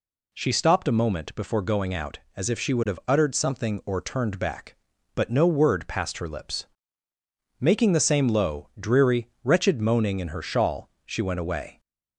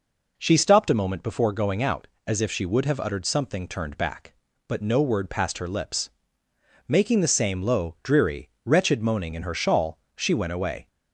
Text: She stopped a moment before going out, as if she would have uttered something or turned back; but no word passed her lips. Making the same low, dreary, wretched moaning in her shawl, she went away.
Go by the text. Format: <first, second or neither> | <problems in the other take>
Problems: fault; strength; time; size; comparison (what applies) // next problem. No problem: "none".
first | skips "or"; at 3.6 s